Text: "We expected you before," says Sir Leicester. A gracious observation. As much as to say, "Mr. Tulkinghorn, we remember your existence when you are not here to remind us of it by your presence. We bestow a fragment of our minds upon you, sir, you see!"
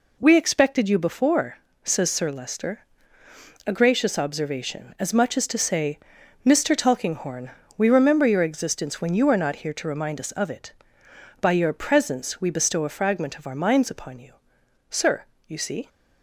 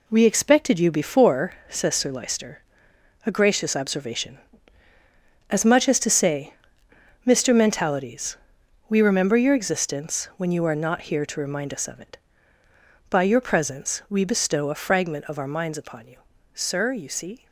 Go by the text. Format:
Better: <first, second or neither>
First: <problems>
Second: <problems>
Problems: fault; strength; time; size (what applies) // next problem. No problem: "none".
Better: first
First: none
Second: says "Mentalities" for "Tulkinghorn"; at 7.5 s